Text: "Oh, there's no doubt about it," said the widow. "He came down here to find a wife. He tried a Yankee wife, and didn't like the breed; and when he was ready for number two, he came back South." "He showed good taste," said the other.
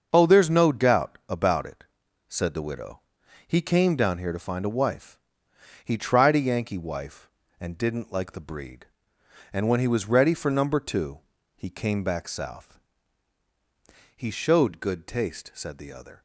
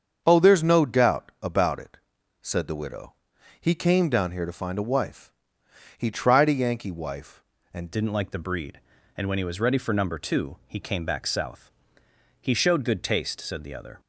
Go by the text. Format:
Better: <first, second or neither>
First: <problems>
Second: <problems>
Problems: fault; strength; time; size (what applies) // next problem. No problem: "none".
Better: first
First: starts louder than the rest; until 1.1 s; 6.5 dB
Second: starts louder than the rest; strong; until 1.2 s; 7.5 dB // changes voice at "didn't"; from 7.9 s on; 6.0 s long